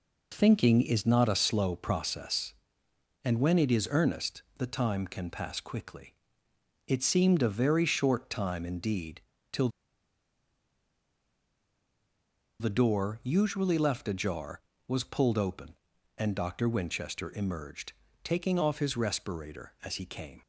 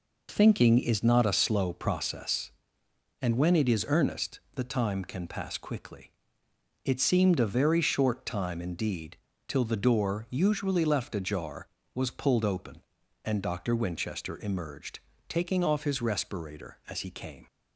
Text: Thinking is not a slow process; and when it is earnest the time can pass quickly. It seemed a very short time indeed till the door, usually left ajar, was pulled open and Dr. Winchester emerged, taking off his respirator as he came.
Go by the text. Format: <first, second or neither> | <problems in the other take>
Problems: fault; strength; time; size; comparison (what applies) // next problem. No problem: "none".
second | pauses between "earnest" and "the"; slight; at 4.4 s; 0.16 s long; slight in the second // pauses between "indeed" and "till"; slight; at 9.2 s; 0.30 s long; slight in the second // pauses between "till" and "the"; strong; at 9.6 s; 2.9 s long